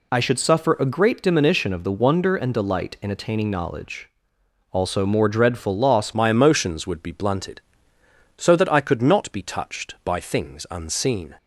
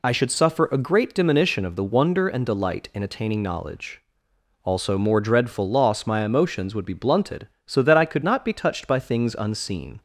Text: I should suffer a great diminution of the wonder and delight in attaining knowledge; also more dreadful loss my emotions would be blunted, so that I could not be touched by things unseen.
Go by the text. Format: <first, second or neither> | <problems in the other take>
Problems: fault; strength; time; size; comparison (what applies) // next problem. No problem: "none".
second | changes voice at "my"; from 6.1 s on; 5.2 s long